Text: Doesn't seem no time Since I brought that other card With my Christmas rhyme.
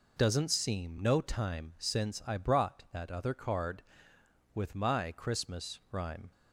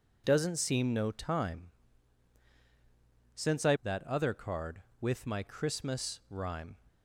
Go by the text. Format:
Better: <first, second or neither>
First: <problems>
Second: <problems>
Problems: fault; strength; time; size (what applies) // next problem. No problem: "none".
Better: first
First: none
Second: pauses between "time" and "Since"; strong; at 1.6 s; 1.6 s long // skips "brought"; at 3.7 s